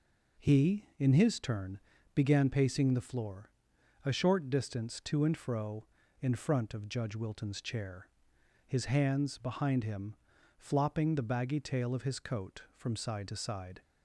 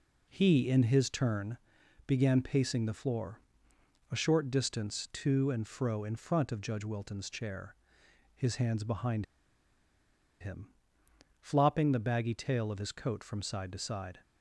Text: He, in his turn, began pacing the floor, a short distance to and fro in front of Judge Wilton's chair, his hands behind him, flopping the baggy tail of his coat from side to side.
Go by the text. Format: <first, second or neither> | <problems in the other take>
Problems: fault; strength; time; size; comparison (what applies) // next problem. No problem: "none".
first | pauses between "behind" and "him"; at 9.2 s; 1.1 s long